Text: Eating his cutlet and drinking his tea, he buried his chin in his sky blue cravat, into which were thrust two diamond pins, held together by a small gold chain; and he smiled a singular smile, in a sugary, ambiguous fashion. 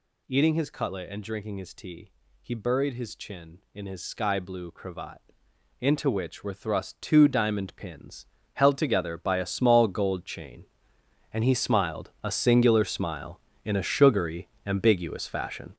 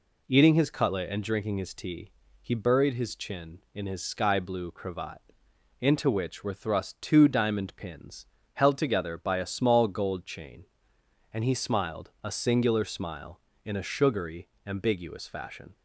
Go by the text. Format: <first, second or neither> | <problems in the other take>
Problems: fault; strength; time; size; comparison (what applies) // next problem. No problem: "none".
second | gets louder; strong; throughout; 8.5 dB